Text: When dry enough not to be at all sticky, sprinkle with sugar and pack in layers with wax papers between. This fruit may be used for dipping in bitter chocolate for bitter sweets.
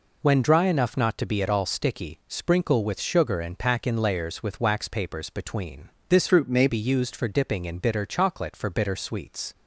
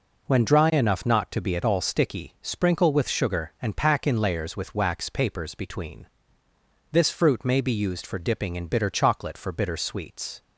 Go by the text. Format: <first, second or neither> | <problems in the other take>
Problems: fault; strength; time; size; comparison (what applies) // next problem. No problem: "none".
second | changes voice from "fruit" to "may"; from 6.2 to 6.6 s; 0.4 s long